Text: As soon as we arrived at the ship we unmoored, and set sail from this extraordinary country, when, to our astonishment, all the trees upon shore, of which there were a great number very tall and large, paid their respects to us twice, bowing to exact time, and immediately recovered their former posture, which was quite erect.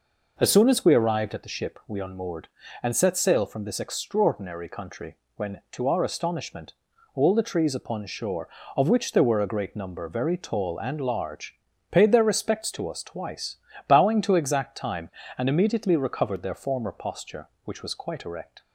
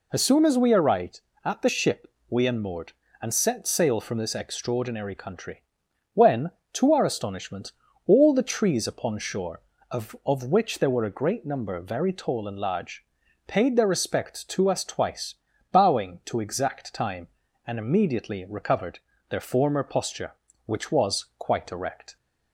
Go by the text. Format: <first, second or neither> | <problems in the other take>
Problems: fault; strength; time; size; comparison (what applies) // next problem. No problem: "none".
first | pauses between "ship" and "we"; slight; at 2.0 s; 0.18 s long // says "of" twice; at 10.2 s // pauses between "recovered" and "their"; slight; at 18.9 s; 0.32 s long